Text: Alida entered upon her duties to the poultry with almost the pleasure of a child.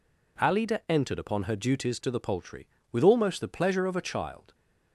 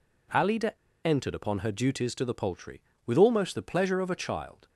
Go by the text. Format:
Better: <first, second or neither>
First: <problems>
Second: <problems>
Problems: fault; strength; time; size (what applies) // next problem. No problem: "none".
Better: first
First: none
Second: pauses between "Alida" and "entered"; slight; at 0.7 s; 0.27 s long